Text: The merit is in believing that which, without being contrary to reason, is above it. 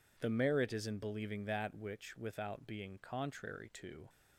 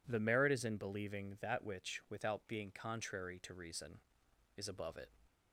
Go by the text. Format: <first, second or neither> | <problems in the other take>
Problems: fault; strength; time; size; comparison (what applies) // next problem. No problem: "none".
second | stops before "reason is above it"; at 4.0 s